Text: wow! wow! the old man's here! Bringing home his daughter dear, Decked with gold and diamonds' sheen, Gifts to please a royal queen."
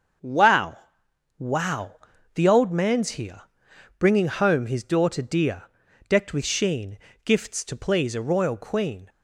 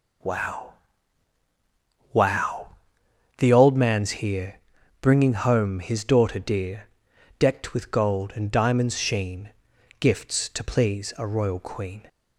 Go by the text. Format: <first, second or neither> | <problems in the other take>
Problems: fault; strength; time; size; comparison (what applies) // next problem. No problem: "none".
second | starts louder than the rest; until 1.8 s; 6.5 dB // skips "gold and diamonds"; at 6.4 s